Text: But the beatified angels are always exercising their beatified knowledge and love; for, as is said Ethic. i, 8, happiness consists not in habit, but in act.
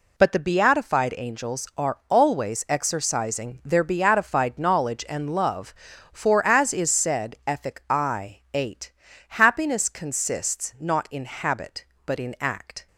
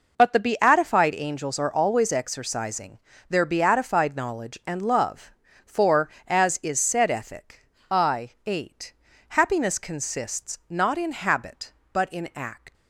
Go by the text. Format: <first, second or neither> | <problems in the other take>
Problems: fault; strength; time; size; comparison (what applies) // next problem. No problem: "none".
first | pauses between "exercising" and "their"; slight; at 2.9 s; 0.30 s long // leaves "act" unfinished; at 12.7 s; 170 ms